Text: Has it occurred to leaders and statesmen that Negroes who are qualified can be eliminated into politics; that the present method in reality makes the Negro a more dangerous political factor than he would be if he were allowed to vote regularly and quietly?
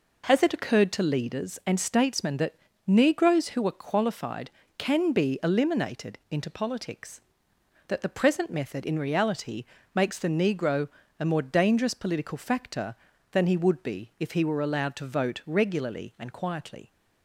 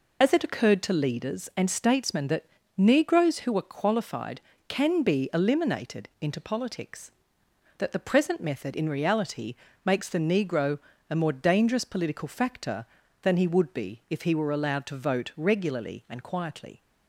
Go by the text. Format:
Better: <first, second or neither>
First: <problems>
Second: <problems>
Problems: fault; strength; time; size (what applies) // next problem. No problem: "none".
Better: first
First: pauses between "that" and "Negroes"; slight; at 2.5 s; 0.32 s long // pauses between "reality" and "makes"; slight; at 9.6 s; 0.28 s long // pauses between "Negro" and "a"; slight; at 10.8 s; 0.30 s long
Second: loses the start of "Has"; at 0.2 s; 65 ms // pauses between "that" and "Negroes"; slight; at 2.4 s; 0.32 s long // pauses between "reality" and "makes"; slight; at 9.5 s; 0.28 s long // pauses between "Negro" and "a"; slight; at 10.7 s; 0.30 s long